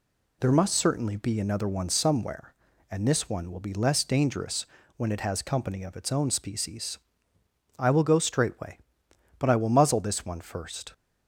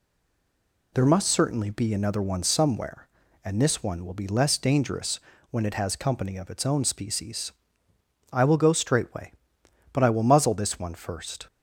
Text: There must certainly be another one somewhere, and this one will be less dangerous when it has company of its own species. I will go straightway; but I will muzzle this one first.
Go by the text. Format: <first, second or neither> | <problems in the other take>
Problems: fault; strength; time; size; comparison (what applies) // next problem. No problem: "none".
first | stays silent before the first word; slight; until 0.9 s; 0.9 s long // pauses between "dangerous" and "when"; slight; at 5.1 s; 0.32 s long; slight in the first